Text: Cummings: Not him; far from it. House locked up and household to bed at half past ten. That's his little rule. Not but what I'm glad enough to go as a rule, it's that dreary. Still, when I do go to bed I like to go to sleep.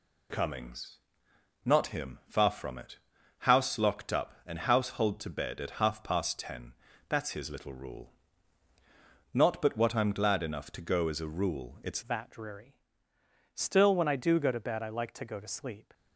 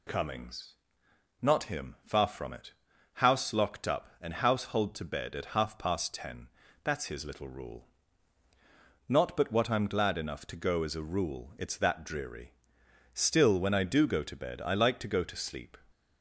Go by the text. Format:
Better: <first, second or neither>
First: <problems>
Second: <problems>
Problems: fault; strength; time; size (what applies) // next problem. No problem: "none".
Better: second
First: changes voice at "that"; from 12.0 s on; 3.9 s long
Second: none